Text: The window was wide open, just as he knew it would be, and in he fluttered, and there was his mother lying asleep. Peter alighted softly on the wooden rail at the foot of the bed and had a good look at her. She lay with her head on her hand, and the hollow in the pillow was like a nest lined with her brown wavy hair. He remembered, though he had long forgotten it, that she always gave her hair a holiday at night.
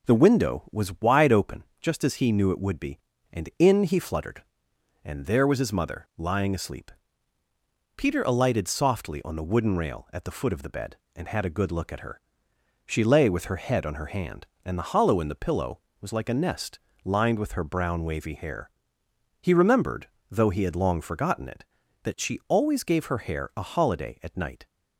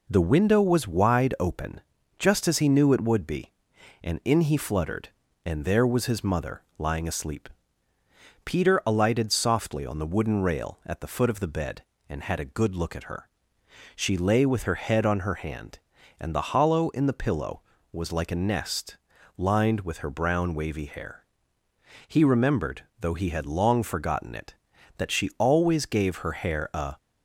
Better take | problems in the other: first | pauses between "mother" and "lying"; slight; at 6.6 s; 0.18 s long // pauses between "nest" and "lined"; at 18.9 s; 0.42 s long; slight in the first // stops before "holiday at night"; at 26.9 s

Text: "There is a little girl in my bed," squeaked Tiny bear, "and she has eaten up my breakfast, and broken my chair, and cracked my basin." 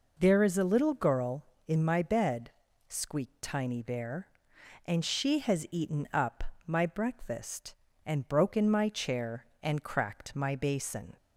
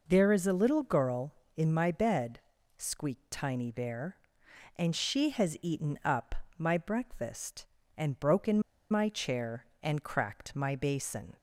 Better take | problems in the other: first | pauses between "up" and "my"; slight; at 6.3 s; 0.22 s long; slight in the first // pauses between "broken" and "my"; slight; at 8.6 s; 0.28 s long

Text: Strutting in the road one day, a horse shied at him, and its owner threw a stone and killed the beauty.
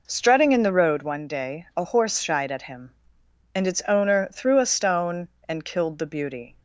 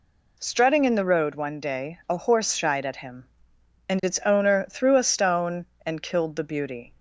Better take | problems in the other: second | starts louder than the rest; noticeable; until 1.2 s; 4.5 dB

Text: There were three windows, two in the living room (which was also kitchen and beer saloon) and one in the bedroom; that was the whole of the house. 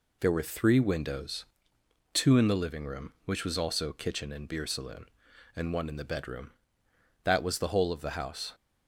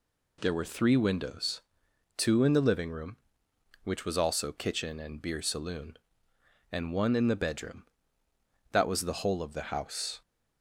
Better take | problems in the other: neither | none

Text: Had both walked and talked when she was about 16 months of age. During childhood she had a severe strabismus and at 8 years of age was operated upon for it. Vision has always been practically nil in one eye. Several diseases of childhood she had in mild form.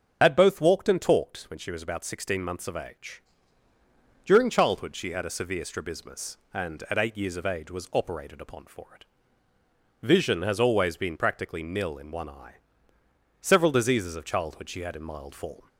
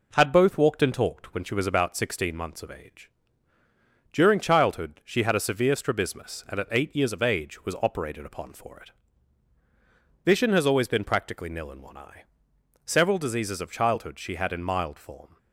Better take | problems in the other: second | loses the start of "Had"; at 0.2 s; 55 ms // starts louder than the rest; until 1.2 s; 7 dB

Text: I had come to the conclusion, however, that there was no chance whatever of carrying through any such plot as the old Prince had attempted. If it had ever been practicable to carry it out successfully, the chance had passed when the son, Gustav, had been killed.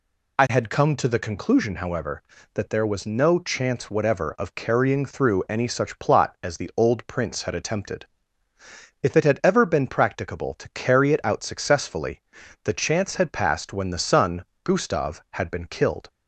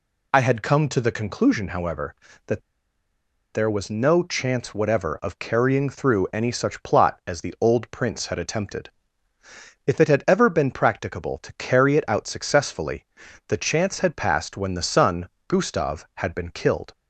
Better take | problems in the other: first | pauses between "that" and "there"; noticeable; at 2.6 s; 0.91 s long

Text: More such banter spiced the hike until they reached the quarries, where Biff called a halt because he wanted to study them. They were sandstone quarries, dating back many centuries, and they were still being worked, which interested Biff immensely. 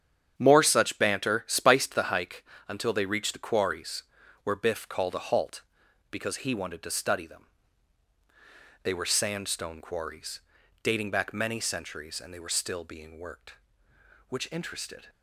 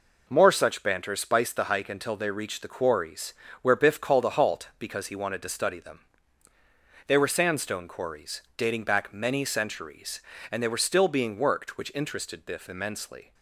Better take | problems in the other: second | starts louder than the rest; strong; until 1.3 s; 8.5 dB // pauses between "hike" and "until"; slight; at 2.4 s; 0.22 s long // stops before "Biff immensely"; at 15.0 s

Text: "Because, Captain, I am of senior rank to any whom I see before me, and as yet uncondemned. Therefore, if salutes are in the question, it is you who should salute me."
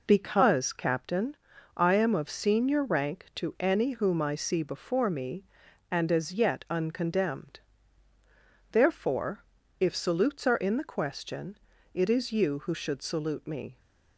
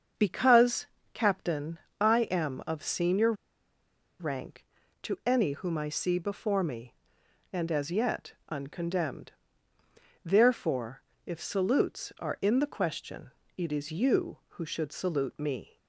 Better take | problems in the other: first | starts louder than the rest; until 1.4 s; 6.5 dB // pauses between "senior" and "rank"; noticeable; at 3.3 s; 0.86 s long // pauses between "yet" and "uncondemned"; slight; at 8.3 s; 0.16 s long

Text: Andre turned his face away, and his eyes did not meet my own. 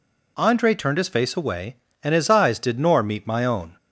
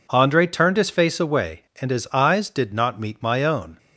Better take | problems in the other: second | says "nor" for "not"; at 2.7 s

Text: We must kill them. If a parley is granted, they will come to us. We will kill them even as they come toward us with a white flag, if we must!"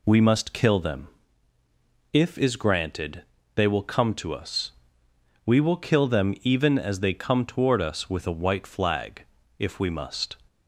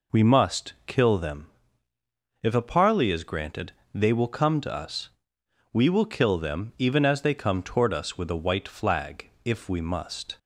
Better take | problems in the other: second | skips "a parley"; at 2.3 s

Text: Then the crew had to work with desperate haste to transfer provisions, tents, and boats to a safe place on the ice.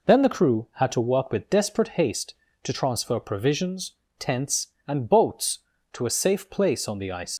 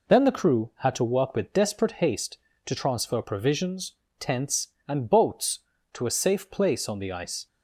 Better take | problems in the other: second | leaves "ice" unfinished; at 7.3 s; 90 ms

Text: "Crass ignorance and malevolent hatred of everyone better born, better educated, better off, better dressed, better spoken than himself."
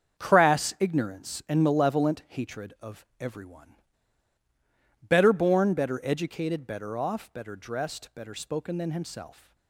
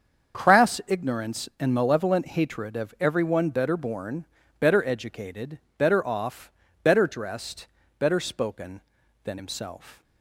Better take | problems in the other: second | starts louder than the rest; strong; until 1.2 s; 7 dB; also in the second // pauses between "of" and "everyone"; slight; at 3.0 s; 0.16 s long // pauses between "everyone" and "better"; strong; at 3.7 s; 1.2 s long

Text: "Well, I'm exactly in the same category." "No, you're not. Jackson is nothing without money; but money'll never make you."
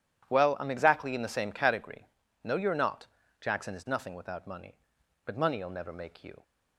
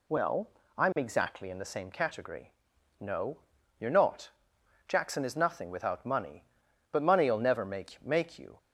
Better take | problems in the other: first | says "make" twice; at 8.0 s

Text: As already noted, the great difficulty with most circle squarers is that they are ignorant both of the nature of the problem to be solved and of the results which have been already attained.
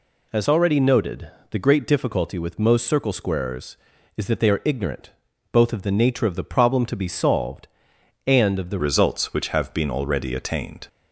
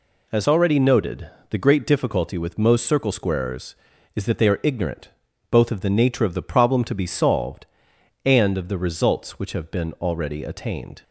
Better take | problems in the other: second | pauses between "ignorant" and "both"; at 5.1 s; 0.40 s long; also in the second // changes voice at "results"; from 8.7 s on; 2.1 s long

